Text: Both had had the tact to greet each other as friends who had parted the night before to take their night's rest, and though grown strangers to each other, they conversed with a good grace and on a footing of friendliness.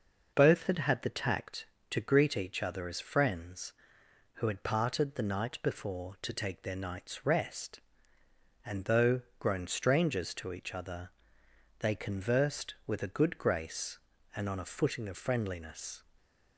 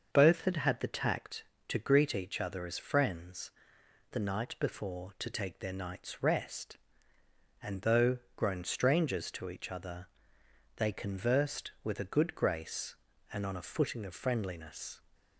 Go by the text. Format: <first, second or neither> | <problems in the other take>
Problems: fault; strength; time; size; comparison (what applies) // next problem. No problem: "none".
first | starts louder than the rest; until 1.1 s; 6.5 dB // skips "who had parted"; at 3.8 s // pauses between "though" and "grown"; slight; at 8.1 s; 0.18 s long; slight in the first